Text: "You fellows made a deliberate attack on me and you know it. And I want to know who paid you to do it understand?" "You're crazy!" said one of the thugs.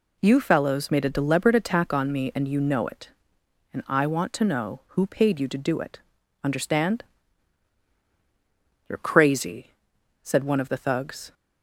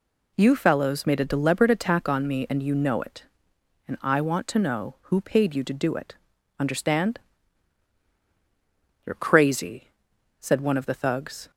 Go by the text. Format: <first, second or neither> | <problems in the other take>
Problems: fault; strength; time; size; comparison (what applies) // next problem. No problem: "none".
neither | pauses between "it" and "understand"; the same in both